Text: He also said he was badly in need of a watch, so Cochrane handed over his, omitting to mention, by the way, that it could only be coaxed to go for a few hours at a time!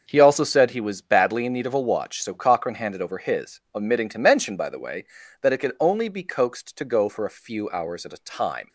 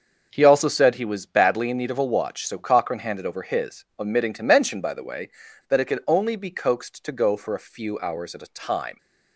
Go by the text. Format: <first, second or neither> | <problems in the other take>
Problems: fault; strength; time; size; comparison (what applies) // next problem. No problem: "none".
neither | starts louder than the rest; the same in both